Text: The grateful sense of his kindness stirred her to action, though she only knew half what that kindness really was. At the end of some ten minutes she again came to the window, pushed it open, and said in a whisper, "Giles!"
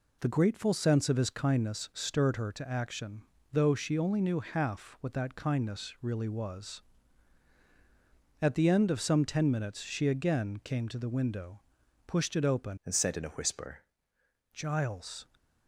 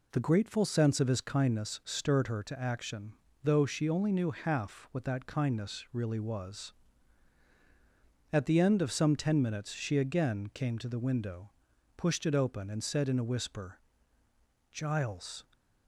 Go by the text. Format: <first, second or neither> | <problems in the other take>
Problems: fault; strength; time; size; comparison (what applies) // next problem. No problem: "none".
second | changes voice from "and" to "whisper"; from 12.8 to 13.8 s; 1.0 s long